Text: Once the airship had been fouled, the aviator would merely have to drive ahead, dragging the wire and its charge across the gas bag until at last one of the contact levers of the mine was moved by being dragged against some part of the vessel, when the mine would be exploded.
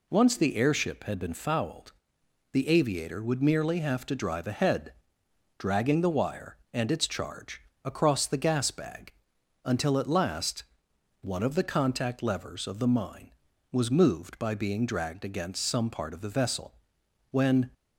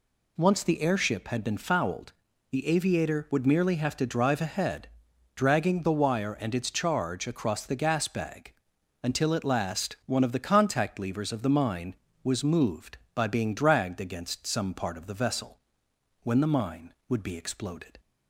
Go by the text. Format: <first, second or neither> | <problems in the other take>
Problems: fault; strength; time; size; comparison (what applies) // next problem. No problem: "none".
second | pauses between "charge" and "across"; slight; at 7.6 s; 0.22 s long // pauses between "bag" and "until"; noticeable; at 9.1 s; 0.52 s long; noticeable in the second // pauses between "last" and "one"; noticeable; at 10.6 s; 0.60 s long // stops before "the mine would be exploded"; at 17.7 s